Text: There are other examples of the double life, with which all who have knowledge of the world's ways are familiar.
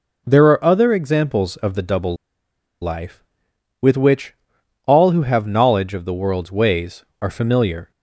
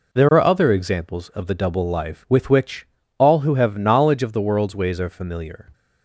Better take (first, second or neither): second